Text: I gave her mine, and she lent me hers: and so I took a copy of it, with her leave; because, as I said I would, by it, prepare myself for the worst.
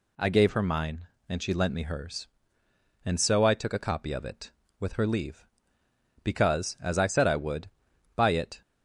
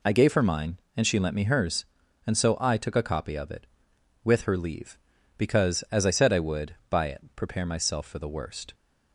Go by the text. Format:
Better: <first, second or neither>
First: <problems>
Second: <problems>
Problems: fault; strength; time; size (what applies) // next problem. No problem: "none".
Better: second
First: stops before "prepare myself for the worst"; at 8.6 s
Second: none